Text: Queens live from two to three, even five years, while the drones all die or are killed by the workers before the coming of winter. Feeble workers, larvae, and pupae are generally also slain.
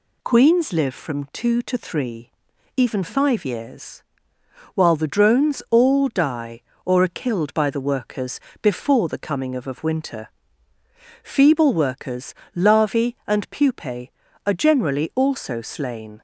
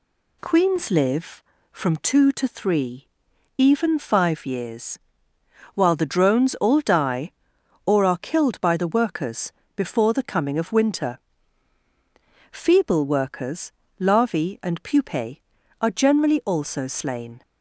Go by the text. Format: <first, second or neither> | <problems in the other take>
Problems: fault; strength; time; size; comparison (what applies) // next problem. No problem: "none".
second | pauses between "workers" and "before"; slight; at 8.3 s; 0.22 s long; slight in the second // says "of" twice; at 9.6 s